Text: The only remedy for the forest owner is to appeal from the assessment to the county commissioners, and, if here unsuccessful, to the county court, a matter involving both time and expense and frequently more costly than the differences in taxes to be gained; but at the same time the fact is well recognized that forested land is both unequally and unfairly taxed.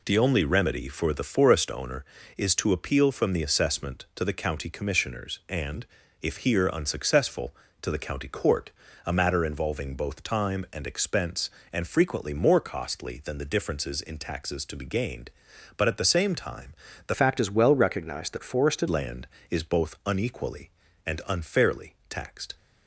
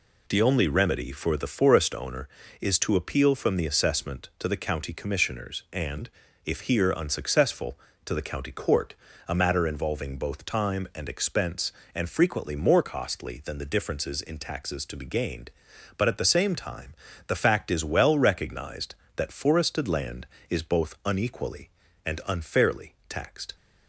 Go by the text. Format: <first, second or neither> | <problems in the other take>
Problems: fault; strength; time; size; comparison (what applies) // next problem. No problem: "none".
second | pauses between "time" and "the"; slight; at 16.7 s; 0.34 s long; slight in the second // changes voice from "fact" to "forested"; from 17.1 to 18.8 s; 1.7 s long